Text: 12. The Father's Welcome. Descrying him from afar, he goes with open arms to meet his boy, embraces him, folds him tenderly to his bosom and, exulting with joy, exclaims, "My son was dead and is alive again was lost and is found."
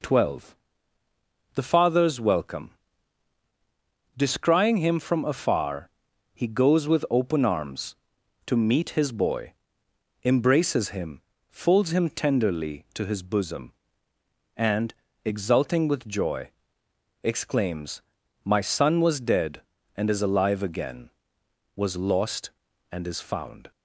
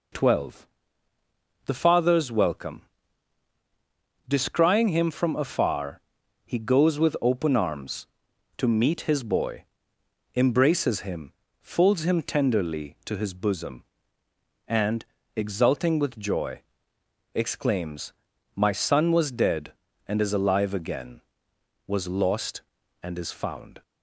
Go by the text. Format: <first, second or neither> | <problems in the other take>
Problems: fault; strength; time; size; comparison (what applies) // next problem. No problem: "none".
neither | none